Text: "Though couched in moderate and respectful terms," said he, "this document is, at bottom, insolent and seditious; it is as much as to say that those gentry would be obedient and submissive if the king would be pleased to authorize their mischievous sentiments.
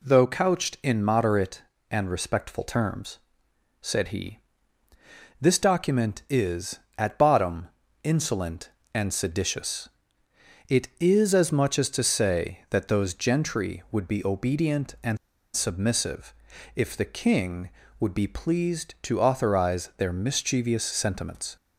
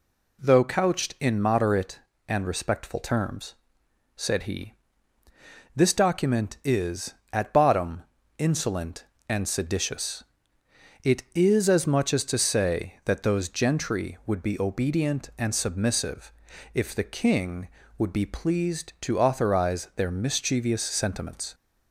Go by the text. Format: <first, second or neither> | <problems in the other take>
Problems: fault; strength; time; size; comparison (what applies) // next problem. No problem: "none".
second | pauses between "and" and "submissive"; at 15.1 s; 0.38 s long // pauses between "submissive" and "if"; at 16.3 s; 0.40 s long; also in the second